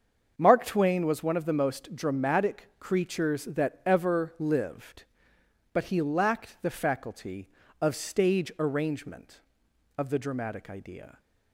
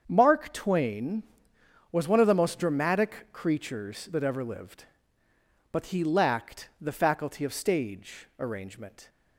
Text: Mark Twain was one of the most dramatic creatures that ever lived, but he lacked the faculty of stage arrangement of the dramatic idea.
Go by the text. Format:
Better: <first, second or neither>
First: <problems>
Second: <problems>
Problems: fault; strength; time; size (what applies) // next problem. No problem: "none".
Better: first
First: starts louder than the rest; until 1.3 s; 7 dB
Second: starts louder than the rest; strong; until 1.0 s; 7 dB // stops before "of the dramatic idea"; at 9.0 s